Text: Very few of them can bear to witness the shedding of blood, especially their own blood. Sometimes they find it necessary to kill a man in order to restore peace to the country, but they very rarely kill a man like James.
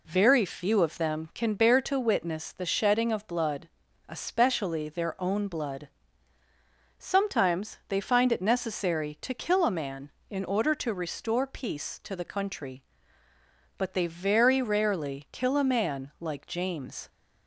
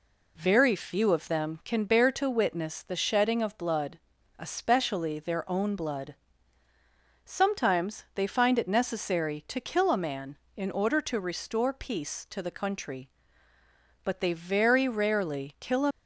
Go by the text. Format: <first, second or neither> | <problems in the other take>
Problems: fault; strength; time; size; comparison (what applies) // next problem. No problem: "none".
first | stops before "man like James"; at 15.9 s